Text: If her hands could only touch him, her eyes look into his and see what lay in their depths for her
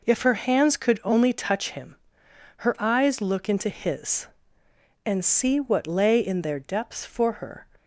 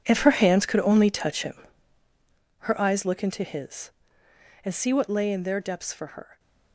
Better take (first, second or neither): first